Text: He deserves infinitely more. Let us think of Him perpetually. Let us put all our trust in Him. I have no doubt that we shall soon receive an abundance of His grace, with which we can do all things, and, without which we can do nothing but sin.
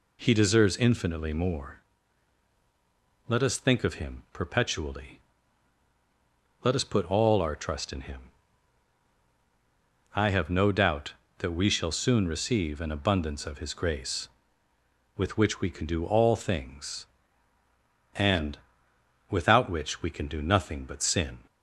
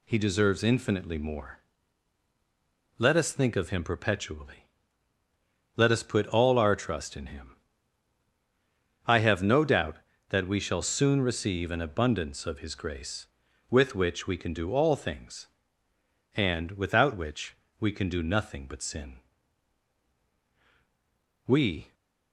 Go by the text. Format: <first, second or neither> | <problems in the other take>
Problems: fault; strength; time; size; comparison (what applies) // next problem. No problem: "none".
first | pauses between "which" and "we"; slight; at 17.5 s; 0.24 s long // goes on to say "We"; slight; from 21.4 s on; 0.46 s long